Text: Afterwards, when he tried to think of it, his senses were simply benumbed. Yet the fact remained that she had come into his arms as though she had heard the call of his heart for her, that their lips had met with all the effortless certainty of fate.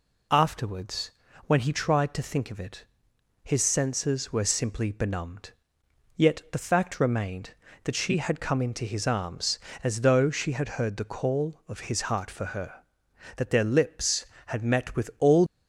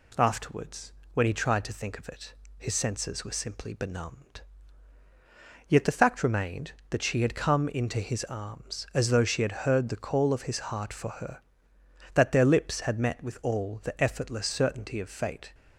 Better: second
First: stops before "the effortless certainty of fate"; at 15.4 s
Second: none

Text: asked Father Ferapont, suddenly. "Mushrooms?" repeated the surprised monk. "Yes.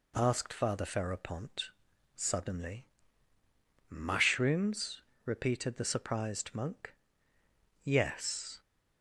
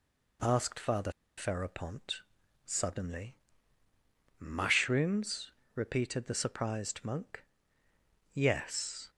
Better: first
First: none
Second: pauses between "Father" and "Ferapont"; slight; at 1.1 s; 0.26 s long

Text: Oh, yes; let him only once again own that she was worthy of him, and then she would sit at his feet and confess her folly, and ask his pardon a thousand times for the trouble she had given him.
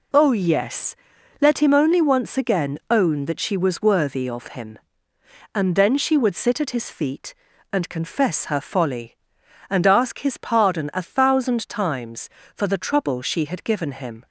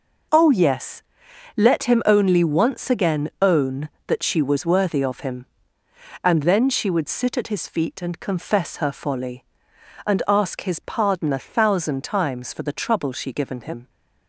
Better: first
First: none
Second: skips "had"; at 13.3 s

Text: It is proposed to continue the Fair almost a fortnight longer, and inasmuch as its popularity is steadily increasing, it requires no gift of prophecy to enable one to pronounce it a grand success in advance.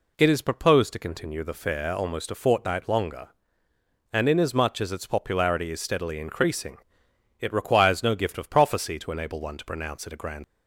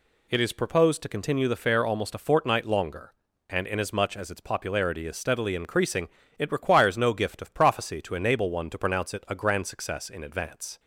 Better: second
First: stops before "success in advance"; at 10.4 s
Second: none

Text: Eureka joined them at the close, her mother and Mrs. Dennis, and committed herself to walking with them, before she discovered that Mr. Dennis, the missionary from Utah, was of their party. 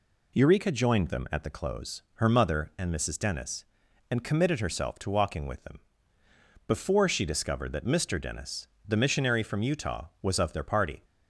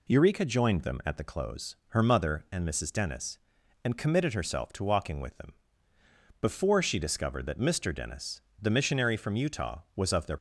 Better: first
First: none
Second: stops before "party"; at 10.3 s

